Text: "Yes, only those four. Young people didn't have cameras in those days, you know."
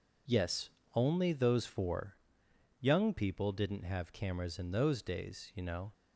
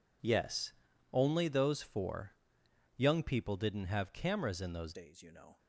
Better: first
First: none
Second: changes voice at "days"; from 4.9 s on; 0.6 s long

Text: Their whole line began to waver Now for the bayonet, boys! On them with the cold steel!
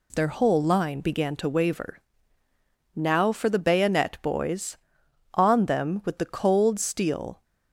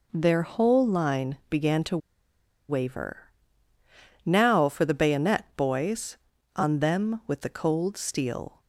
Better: first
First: pauses between "waver" and "Now"; noticeable; at 1.9 s; 0.96 s long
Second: pauses between "to" and "waver"; noticeable; at 1.9 s; 0.71 s long // pauses between "waver" and "Now"; noticeable; at 3.2 s; 0.94 s long

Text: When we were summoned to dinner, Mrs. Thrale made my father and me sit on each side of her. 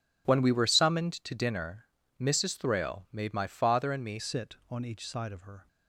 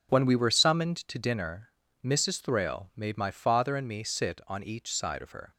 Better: second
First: changes voice at "sit"; from 4.1 s on; 1.5 s long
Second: none

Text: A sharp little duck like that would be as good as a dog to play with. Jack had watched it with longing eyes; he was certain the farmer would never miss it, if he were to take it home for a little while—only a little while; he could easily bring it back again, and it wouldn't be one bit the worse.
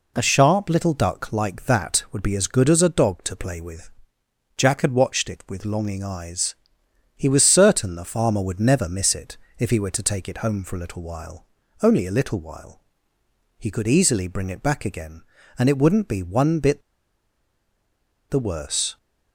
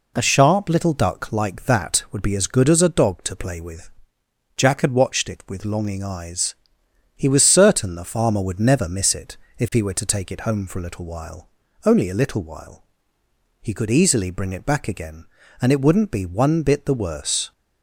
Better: second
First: pauses between "bit" and "the"; strong; at 16.8 s; 1.4 s long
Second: none

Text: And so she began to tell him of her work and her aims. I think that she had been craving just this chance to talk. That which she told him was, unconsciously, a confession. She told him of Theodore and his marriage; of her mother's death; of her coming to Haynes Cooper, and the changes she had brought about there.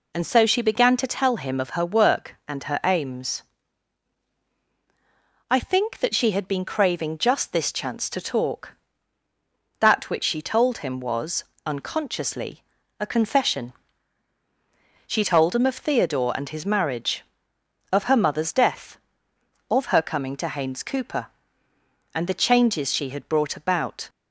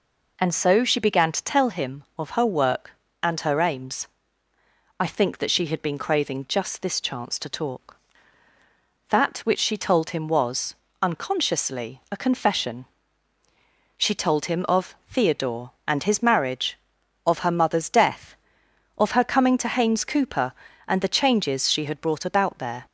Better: second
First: stops before "there"; at 24.0 s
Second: none

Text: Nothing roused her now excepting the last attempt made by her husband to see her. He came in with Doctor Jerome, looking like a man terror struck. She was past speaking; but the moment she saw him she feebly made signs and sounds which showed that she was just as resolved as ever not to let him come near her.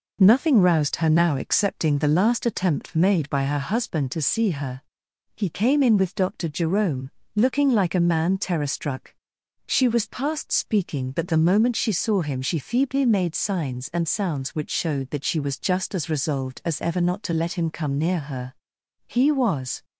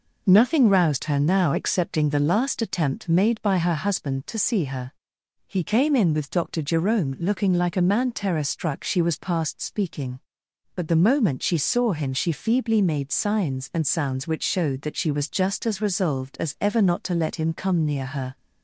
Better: second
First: goes on to say "He was"; noticeable; from 19.0 s on; 0.78 s long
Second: none

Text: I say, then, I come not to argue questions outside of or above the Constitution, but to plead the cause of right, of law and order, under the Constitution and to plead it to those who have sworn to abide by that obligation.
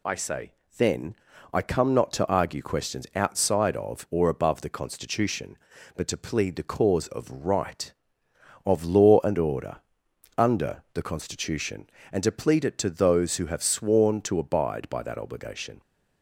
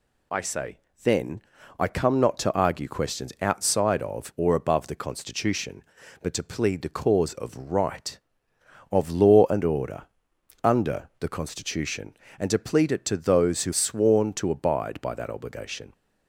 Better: first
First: none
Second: skips "have"; at 13.7 s

